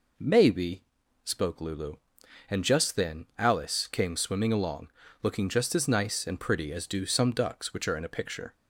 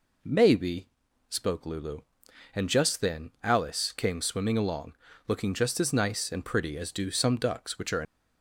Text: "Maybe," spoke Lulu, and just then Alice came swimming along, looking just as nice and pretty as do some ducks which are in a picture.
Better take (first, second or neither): first